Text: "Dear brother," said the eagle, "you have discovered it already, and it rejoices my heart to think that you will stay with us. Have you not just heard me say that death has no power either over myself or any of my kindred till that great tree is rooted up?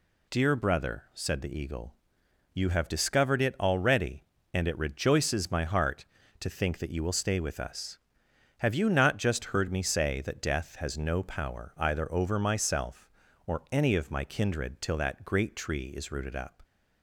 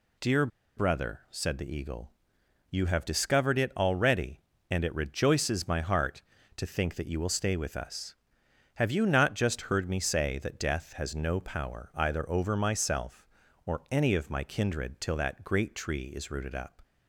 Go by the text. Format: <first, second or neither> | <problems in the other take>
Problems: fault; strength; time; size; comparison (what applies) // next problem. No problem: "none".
first | pauses between "Dear" and "brother"; slight; at 0.4 s; 0.29 s long